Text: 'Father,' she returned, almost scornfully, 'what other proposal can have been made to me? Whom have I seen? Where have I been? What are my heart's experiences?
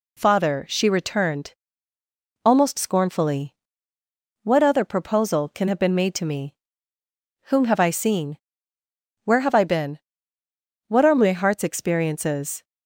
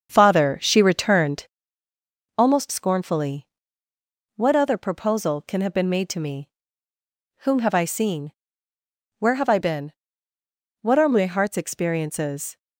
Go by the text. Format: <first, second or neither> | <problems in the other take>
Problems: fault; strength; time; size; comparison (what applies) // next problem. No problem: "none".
first | starts louder than the rest; strong; until 1.7 s; 7 dB